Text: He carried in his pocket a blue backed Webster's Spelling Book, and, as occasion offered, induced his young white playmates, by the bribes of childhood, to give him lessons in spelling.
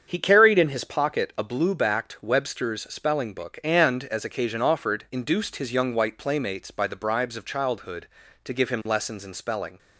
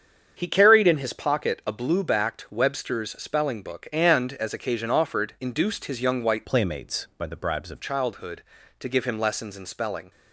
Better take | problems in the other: first | starts louder than the rest; strong; until 1.3 s; 7.5 dB; strong in the first // changes voice from "playmates" to "of"; from 6.4 to 7.8 s; 1.4 s long

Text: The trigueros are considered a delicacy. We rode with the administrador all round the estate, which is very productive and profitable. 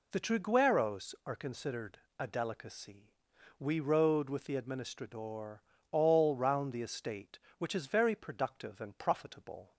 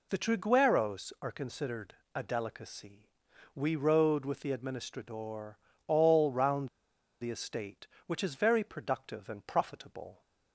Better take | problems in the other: first | pauses between "considered" and "a"; slight; at 1.9 s; 0.20 s long; slight in the first // pauses between "administrador" and "all"; slight; at 5.5 s; 0.30 s long; slight in the first // pauses between "round" and "the"; noticeable; at 6.6 s; 0.52 s long

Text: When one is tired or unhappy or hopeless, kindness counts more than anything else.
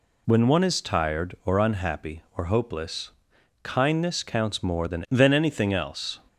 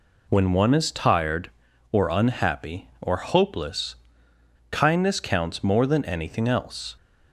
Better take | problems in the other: second | says "than" twice; at 5.1 s

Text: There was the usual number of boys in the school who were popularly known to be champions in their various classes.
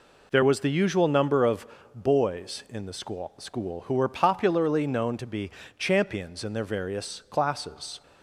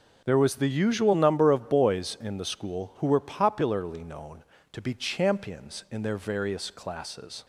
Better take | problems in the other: second | pauses between "of" and "boys"; slight; at 1.6 s; 0.28 s long // says "school" twice; at 3.3 s // pauses between "be" and "champions"; slight; at 5.5 s; 0.28 s long

